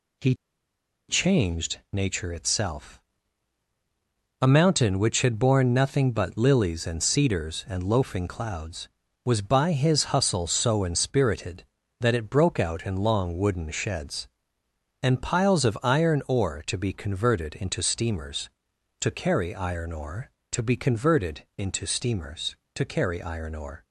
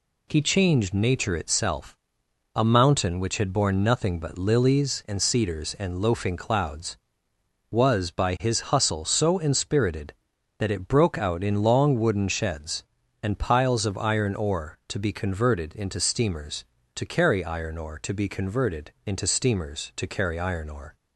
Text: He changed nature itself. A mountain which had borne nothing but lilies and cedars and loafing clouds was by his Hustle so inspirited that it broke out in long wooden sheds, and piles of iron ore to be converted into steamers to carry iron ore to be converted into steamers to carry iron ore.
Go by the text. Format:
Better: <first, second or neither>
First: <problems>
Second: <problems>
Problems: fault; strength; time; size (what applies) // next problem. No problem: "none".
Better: second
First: pauses between "He" and "changed"; noticeable; at 0.3 s; 0.74 s long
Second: none